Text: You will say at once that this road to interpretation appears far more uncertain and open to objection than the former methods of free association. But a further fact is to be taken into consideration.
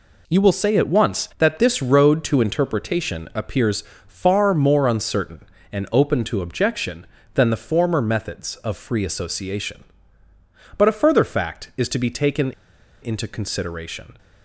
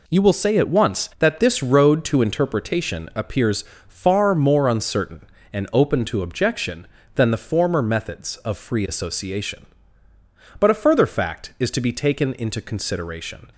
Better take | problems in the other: second | pauses between "appears" and "far"; slight; at 3.8 s; 0.24 s long; slight in the second // pauses between "taken" and "into"; noticeable; at 12.5 s; 0.50 s long

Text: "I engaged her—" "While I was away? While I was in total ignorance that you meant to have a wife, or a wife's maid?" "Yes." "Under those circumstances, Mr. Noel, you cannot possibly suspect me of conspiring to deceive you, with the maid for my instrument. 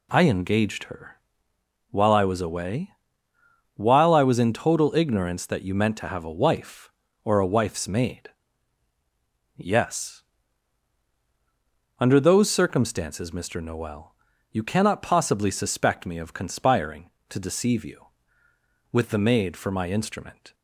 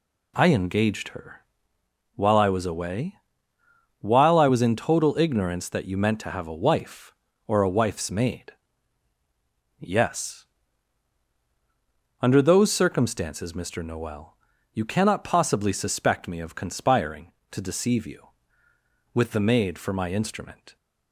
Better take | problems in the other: neither | none

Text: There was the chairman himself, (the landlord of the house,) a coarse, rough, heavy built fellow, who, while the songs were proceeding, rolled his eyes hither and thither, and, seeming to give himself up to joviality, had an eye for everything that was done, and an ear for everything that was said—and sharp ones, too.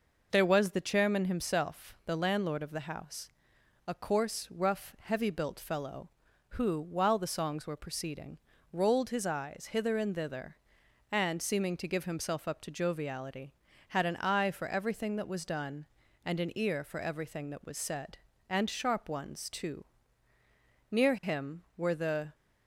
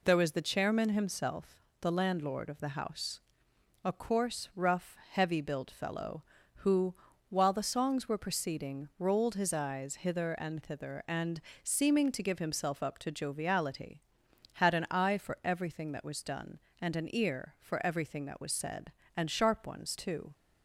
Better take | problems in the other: second | goes on to say "Near him were the"; from 20.9 s on; 1.4 s long

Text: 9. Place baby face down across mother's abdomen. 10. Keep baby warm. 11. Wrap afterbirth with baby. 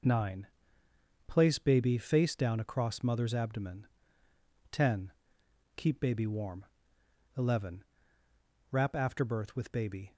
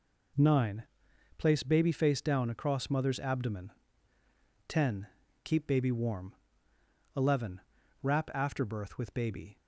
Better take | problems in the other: neither | none

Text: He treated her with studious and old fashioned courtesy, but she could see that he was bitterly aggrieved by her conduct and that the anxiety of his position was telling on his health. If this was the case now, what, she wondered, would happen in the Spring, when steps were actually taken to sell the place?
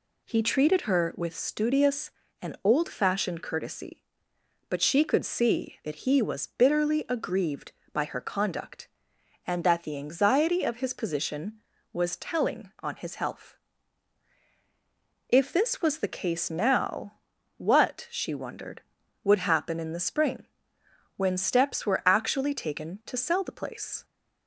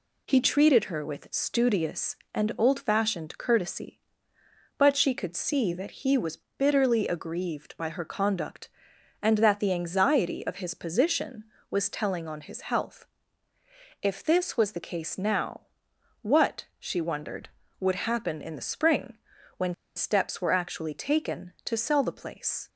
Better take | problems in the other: first | pauses between "was" and "bitterly"; slight; at 6.3 s; 0.18 s long // pauses between "when" and "steps"; slight; at 19.7 s; 0.23 s long

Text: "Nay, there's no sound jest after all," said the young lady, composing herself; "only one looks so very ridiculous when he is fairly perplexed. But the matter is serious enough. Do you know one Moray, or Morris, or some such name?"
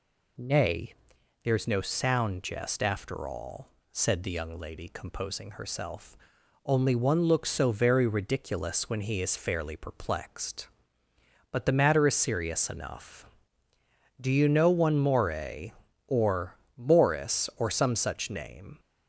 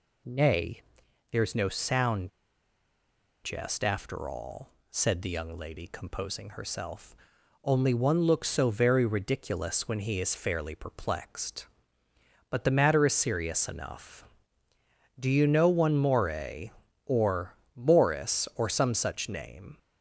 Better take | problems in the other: first | pauses between "sound" and "jest"; at 2.2 s; 1.1 s long // pauses between "or" and "Morris"; slight; at 17.5 s; 0.22 s long; slight in the first

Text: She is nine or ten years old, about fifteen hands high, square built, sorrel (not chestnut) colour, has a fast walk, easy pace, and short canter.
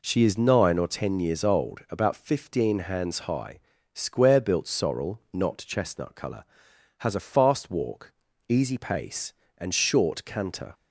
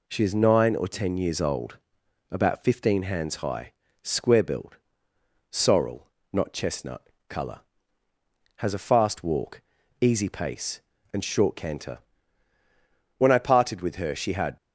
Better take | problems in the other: first | goes on to say "When I parted with her she had"; from 13.1 s on; 1.3 s long

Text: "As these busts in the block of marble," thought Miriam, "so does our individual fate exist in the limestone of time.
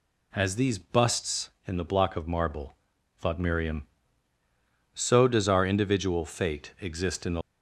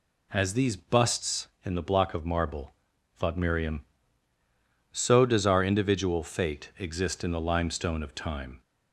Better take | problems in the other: second | stops before "limestone of time"; at 7.4 s

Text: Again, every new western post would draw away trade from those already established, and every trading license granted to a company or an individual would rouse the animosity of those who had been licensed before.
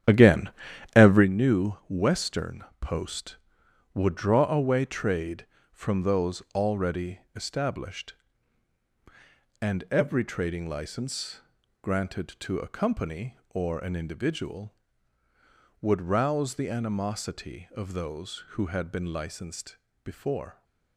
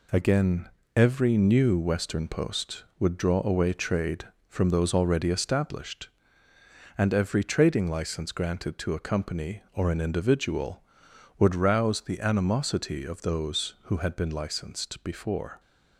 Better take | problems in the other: second | starts louder than the rest; strong; until 1.3 s; 10 dB // pauses between "new" and "western"; slight; at 1.7 s; 0.16 s long // pauses between "western" and "post"; slight; at 2.6 s; 0.16 s long // pauses between "license" and "granted"; at 11.3 s; 0.42 s long // pauses between "licensed" and "before"; slight; at 19.7 s; 0.26 s long

